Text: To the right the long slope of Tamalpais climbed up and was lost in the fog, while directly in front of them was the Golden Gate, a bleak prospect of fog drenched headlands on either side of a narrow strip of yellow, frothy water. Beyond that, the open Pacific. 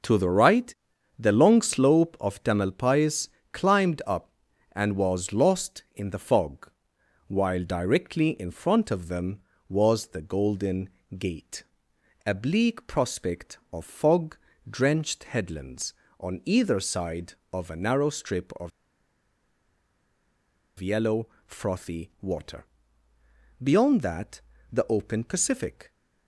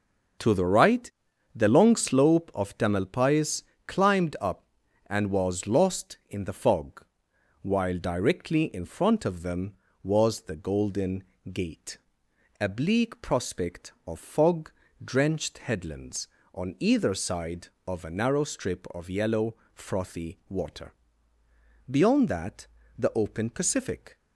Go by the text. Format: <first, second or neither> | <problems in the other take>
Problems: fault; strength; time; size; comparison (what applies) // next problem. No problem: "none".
second | starts louder than the rest; until 1.4 s; 6 dB; also in the second // pauses between "right" and "the"; at 0.7 s; 0.44 s long; also in the second // pauses between "Tamalpais" and "climbed"; slight; at 3.2 s; 0.24 s long; slight in the second // pauses between "Golden" and "Gate"; slight; at 10.8 s; 0.30 s long; slight in the second // pauses between "fog" and "drenched"; slight; at 14.3 s; 0.32 s long; slight in the second // pauses between "of" and "yellow"; strong; at 18.7 s; 2.0 s long